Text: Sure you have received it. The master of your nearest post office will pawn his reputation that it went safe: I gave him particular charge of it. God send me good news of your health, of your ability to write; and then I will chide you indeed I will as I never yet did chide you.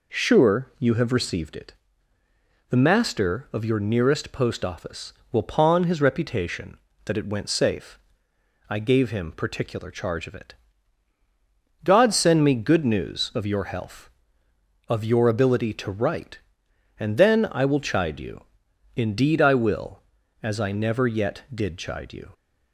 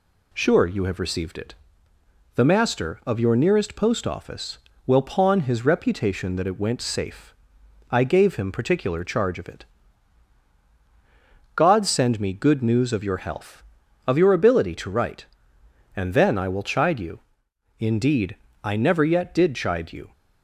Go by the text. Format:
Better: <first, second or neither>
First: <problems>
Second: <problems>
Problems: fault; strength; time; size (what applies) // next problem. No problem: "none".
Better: first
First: pauses between "you" and "indeed"; noticeable; at 18.4 s; 0.54 s long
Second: pauses between "you" and "indeed"; noticeable; at 17.1 s; 0.58 s long // skips "I will as"; at 18.4 s